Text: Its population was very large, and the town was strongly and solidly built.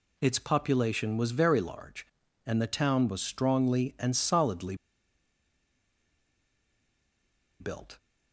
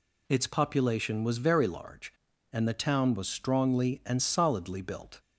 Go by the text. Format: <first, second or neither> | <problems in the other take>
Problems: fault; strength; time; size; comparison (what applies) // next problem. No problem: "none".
second | pauses between "solidly" and "built"; strong; at 4.7 s; 2.8 s long